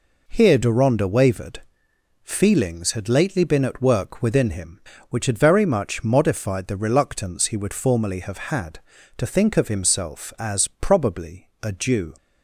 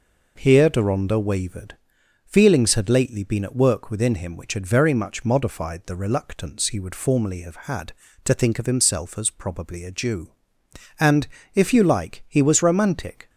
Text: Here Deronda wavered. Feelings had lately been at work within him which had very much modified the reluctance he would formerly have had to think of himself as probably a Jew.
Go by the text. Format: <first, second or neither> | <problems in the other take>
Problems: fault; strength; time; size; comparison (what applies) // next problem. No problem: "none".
first | goes on to say "And if you like he was romantic"; strong; from 10.9 s on; 2.3 s long